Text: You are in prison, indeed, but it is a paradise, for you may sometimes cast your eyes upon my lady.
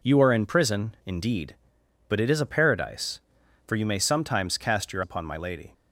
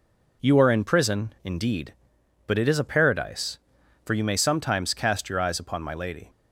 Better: second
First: skips "eyes"; at 5.0 s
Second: none

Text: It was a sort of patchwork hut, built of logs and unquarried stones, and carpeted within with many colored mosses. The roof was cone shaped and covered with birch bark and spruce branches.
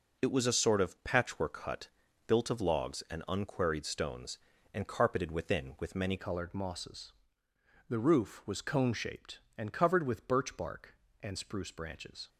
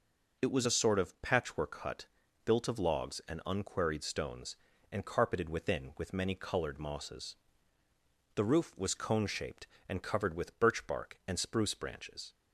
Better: second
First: changes voice at "colored"; from 6.1 s on; 6.1 s long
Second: none

